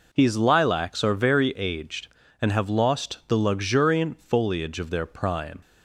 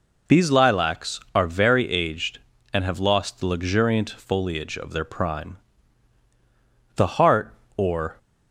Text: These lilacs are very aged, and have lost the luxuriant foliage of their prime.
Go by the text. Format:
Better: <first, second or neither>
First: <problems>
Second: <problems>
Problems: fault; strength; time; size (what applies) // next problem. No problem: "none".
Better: first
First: none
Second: goes on to say "The heart or"; noticeable; from 6.9 s on; 1.2 s long